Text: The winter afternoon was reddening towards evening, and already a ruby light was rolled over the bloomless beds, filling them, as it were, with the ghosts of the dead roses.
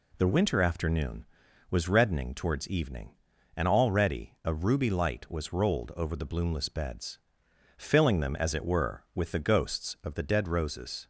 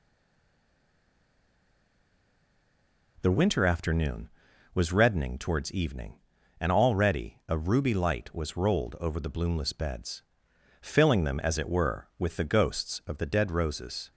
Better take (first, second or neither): first